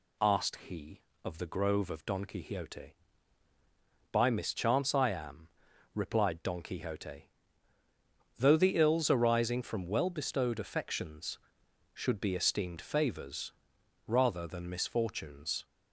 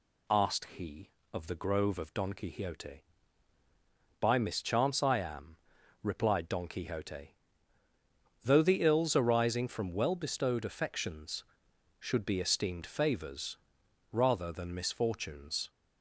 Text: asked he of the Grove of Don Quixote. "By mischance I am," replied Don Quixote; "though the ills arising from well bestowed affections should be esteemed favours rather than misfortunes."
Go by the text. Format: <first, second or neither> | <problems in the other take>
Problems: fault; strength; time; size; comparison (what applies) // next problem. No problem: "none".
neither | pauses between "favours" and "rather"; noticeable; the same in both